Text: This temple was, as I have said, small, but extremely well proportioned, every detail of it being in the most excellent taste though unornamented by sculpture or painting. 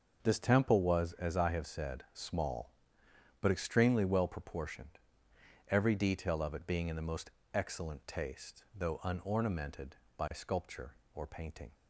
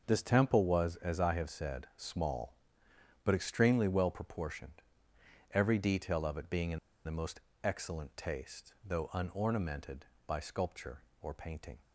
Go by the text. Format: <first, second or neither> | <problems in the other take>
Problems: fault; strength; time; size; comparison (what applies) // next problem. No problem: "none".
first | starts louder than the rest; noticeable; until 1.0 s; 6 dB; noticeable in the first // pauses between "in" and "the"; slight; at 6.7 s; 0.27 s long // pauses between "most" and "excellent"; slight; at 7.3 s; 0.24 s long; slight in the first